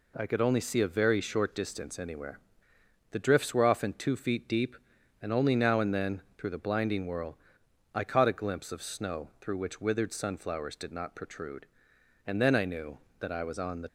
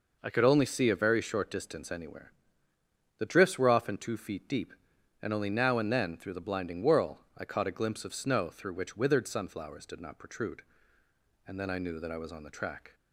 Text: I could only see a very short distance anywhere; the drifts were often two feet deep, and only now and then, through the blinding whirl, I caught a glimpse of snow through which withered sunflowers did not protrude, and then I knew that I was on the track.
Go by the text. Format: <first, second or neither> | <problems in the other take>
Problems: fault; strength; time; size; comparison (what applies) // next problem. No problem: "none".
second | stops before "track"; at 13.8 s